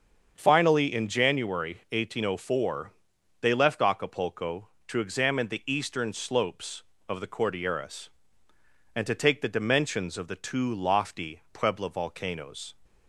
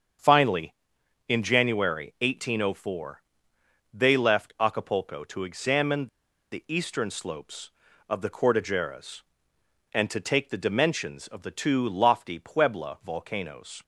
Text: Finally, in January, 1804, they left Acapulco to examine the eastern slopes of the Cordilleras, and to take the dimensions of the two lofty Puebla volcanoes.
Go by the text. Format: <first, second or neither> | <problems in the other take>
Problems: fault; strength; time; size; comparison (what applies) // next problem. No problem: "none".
first | starts louder than the rest; strong; until 1.7 s; 7 dB; also in the first // pauses between "examine" and "the"; at 6.0 s; 0.43 s long